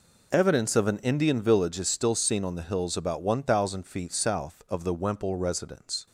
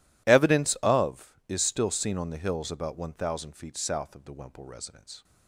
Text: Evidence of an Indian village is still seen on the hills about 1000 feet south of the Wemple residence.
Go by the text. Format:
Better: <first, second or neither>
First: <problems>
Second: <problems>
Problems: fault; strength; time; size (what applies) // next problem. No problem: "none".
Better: first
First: none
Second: skips "an Indian village"; at 1.4 s